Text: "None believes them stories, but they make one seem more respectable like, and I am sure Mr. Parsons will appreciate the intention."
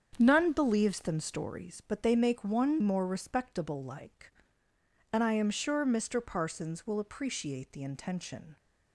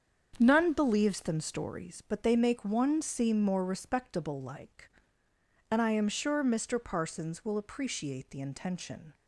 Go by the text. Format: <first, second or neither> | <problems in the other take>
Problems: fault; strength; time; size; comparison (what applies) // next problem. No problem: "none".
second | starts louder than the rest; strong; until 1.2 s; 7.5 dB; strong in the second // skips "seem"; at 2.8 s